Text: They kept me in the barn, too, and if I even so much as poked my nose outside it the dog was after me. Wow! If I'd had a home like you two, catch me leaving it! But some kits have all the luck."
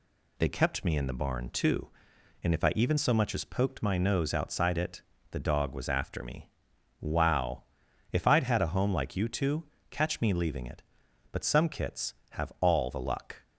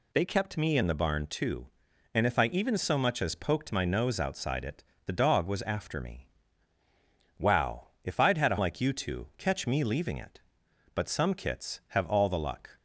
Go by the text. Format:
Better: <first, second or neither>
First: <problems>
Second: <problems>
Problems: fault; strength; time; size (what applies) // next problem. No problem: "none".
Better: first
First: pauses between "it" and "the"; slight; at 5.0 s; 0.30 s long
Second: pauses between "it" and "the"; slight; at 4.8 s; 0.24 s long // skips "home"; at 8.5 s